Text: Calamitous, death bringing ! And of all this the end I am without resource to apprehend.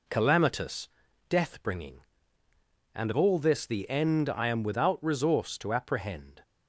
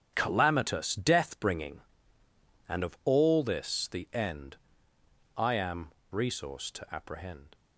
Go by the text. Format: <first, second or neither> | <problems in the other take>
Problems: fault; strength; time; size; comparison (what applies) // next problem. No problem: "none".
first | starts louder than the rest; strong; until 1.1 s; 8 dB // pauses between "end" and "I"; noticeable; at 4.5 s; 0.80 s long // skips "without"; at 6.0 s